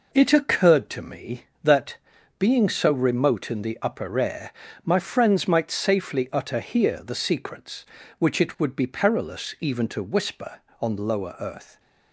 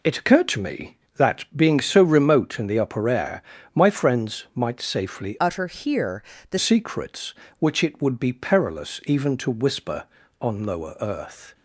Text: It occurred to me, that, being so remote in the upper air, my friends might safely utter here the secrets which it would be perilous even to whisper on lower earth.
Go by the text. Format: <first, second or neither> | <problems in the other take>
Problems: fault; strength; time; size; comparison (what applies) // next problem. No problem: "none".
first | changes voice from "utter" to "the"; from 5.3 to 6.5 s; 1.2 s long // pauses between "here" and "the"; slight; at 6.2 s; 0.28 s long